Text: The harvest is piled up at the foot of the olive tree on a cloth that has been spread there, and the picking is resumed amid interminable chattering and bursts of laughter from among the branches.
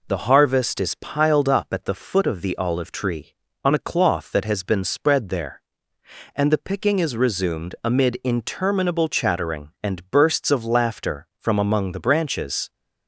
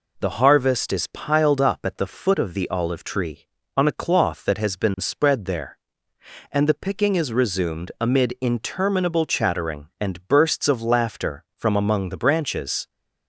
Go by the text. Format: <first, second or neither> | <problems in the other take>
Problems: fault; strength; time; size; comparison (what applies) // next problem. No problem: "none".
neither | none